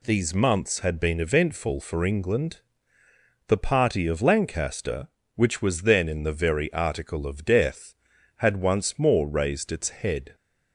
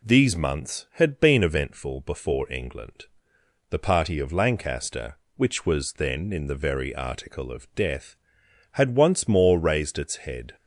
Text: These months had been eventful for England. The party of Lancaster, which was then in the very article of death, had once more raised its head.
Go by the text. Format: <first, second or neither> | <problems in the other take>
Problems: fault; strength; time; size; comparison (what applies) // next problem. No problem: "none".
first | says "before" for "for"; at 2.0 s